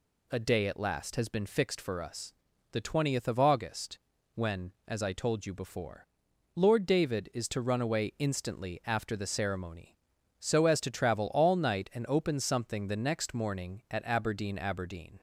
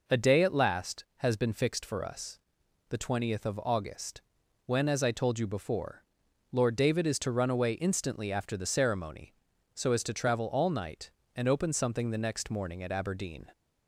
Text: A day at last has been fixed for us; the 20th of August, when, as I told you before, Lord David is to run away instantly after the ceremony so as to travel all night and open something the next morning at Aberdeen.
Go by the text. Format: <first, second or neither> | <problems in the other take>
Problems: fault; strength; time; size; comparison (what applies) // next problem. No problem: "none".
second | says "Aberdeen" twice; at 14.5 s